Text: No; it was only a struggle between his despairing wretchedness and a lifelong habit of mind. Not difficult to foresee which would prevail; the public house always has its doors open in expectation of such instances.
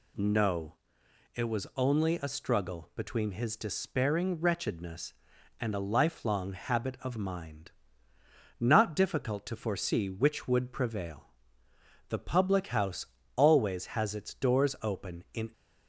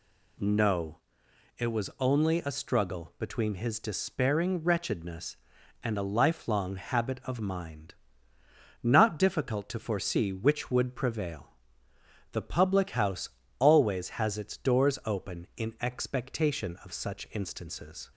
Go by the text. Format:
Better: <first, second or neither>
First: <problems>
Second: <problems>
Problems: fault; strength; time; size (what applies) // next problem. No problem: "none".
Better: second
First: pauses between "house" and "always"; slight; at 13.0 s; 0.28 s long // stops before "expectation of such instances"; at 15.5 s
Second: pauses between "house" and "always"; slight; at 13.2 s; 0.28 s long